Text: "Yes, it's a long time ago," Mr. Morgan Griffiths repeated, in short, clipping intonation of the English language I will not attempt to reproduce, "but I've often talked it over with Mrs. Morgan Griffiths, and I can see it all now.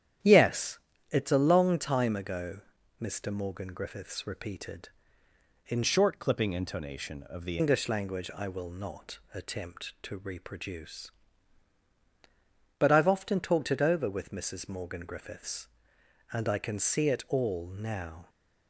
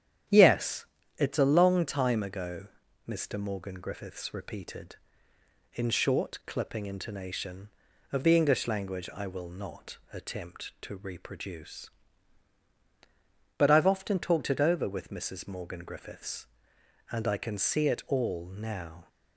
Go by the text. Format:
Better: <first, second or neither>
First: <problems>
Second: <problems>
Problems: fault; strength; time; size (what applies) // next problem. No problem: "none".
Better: second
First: starts louder than the rest; strong; until 1.5 s; 10 dB // changes voice from "short" to "the"; from 5.8 to 7.5 s; 1.7 s long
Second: starts louder than the rest; strong; until 1.6 s; 9.5 dB